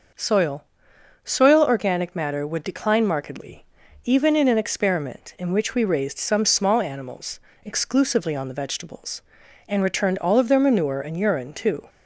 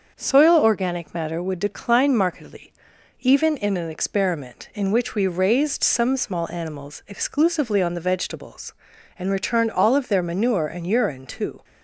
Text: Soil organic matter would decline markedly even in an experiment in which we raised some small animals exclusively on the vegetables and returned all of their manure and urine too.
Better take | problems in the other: second | starts louder than the rest; noticeable; until 1.7 s; 6 dB; also in the second // says "Soil" twice; at 1.2 s // pauses between "markedly" and "even"; at 3.6 s; 0.40 s long; noticeable in the second // pauses between "animals" and "exclusively"; slight; at 7.3 s; 0.26 s long

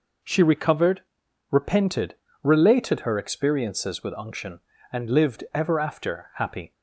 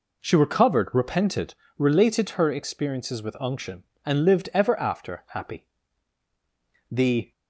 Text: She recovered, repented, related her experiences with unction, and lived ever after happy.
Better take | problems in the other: first | goes on to say "The"; slight; from 6.9 s on; 0.40 s long

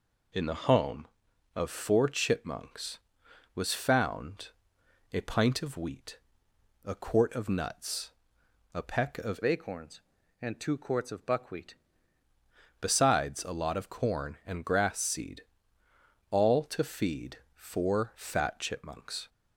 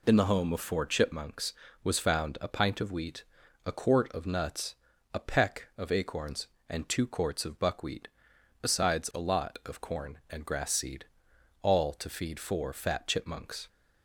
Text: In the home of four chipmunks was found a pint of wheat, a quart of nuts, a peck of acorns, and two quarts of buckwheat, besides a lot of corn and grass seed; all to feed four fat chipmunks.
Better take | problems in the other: second | pauses between "found" and "a"; noticeable; at 4.4 s; 0.64 s long // changes voice from "acorns" to "buckwheat"; from 9.4 to 11.7 s; 2.3 s long // pauses between "feed" and "four"; slight; at 17.3 s; 0.18 s long

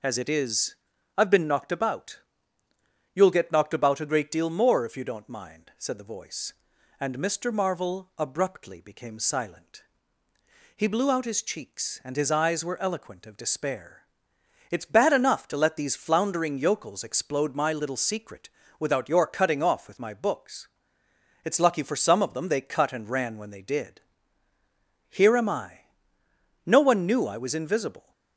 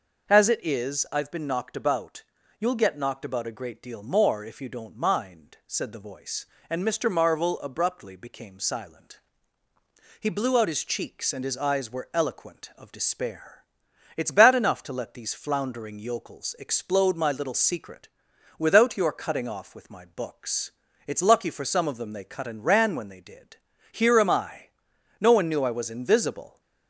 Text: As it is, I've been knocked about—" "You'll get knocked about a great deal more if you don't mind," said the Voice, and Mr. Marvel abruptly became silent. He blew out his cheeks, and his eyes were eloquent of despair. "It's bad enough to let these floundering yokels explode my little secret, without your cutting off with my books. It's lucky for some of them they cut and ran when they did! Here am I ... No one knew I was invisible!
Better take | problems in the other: neither | none

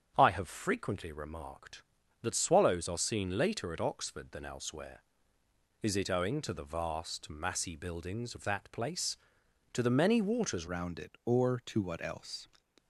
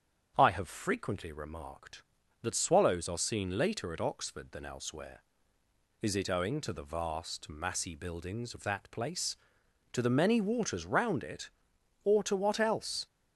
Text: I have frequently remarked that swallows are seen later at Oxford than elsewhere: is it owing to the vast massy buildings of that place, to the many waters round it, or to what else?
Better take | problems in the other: second | starts louder than the rest; strong; until 1.1 s; 8 dB; strong in the second // changes voice at "round"; from 10.6 s on; 1.8 s long

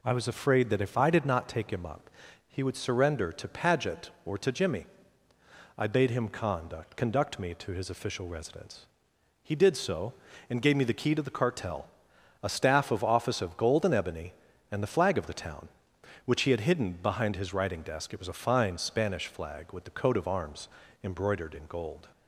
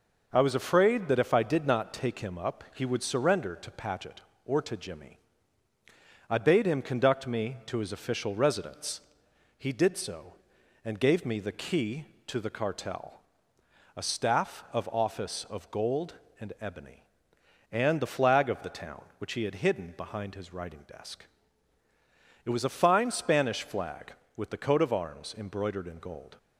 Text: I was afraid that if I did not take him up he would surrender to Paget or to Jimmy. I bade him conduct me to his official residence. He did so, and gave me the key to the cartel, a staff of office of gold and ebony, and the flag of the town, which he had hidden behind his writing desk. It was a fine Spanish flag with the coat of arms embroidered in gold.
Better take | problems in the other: second | pauses between "up" and "he"; at 2.0 s; 0.40 s long // says "conduct" twice; at 6.9 s // pauses between "arms" and "embroidered"; slight; at 20.6 s; 0.34 s long

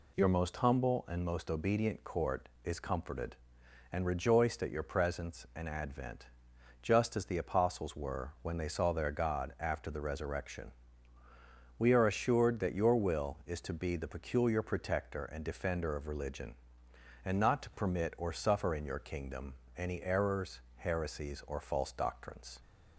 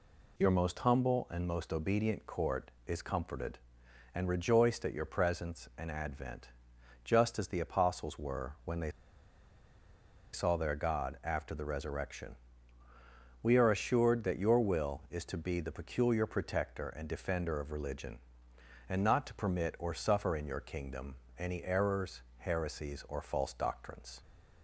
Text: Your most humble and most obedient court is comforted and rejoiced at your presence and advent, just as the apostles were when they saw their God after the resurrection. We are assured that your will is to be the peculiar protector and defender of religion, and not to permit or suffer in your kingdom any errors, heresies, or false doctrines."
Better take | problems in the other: first | pauses between "they" and "saw"; strong; at 8.8 s; 1.4 s long // pauses between "kingdom" and "any"; slight; at 21.1 s; 0.24 s long; slight in the first

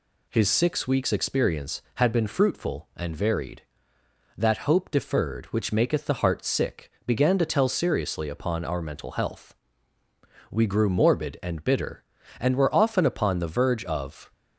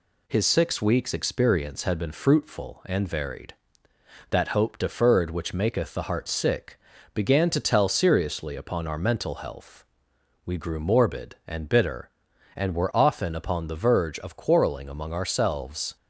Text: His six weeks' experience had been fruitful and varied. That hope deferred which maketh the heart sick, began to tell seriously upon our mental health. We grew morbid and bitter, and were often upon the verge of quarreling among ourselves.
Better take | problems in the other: second | stops before "quarreling among ourselves"; at 14.3 s

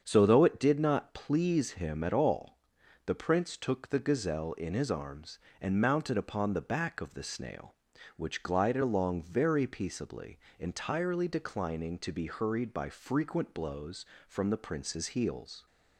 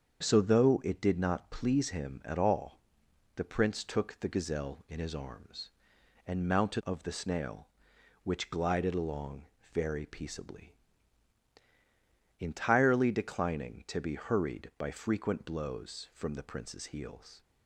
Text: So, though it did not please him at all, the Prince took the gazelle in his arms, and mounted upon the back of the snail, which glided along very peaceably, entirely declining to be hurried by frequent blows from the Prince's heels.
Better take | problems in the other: first | starts louder than the rest; until 1.2 s; 7 dB; strong in the first // skips "upon the back"; at 6.8 s // pauses between "along" and "very"; slight; at 9.4 s; 0.26 s long

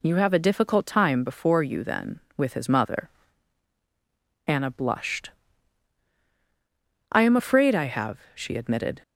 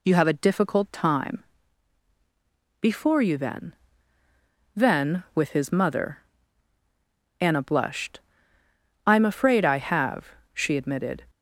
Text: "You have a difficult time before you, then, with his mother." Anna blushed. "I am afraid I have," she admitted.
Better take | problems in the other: first | pauses between "time" and "before"; strong; at 1.4 s; 1.3 s long // says "then" twice; at 4.7 s

